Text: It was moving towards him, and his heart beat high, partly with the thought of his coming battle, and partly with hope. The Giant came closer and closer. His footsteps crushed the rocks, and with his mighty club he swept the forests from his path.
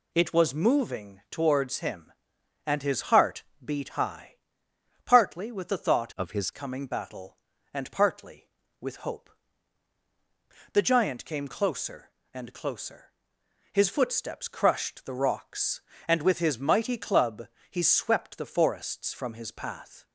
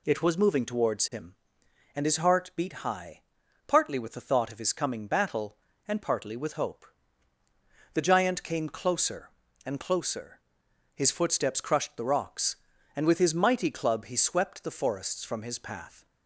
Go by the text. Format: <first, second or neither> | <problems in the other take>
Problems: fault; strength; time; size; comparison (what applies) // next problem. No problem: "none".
second | pauses between "heart" and "beat"; slight; at 3.4 s; 0.20 s long // changes voice from "of" to "his"; from 6.1 to 6.5 s; 0.4 s long // pauses between "club" and "he"; slight; at 17.4 s; 0.22 s long